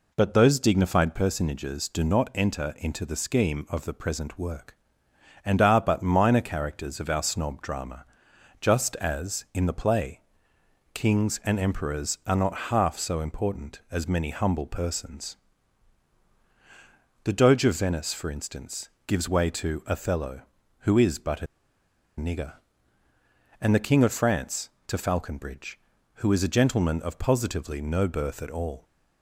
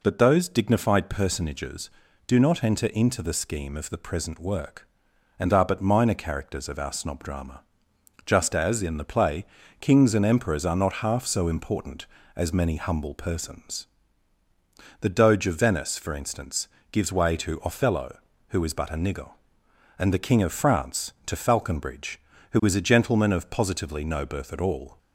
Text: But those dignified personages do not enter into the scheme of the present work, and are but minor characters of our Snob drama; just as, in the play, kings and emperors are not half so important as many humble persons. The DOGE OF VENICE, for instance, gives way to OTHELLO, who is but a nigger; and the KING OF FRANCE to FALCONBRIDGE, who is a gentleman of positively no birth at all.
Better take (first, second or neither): second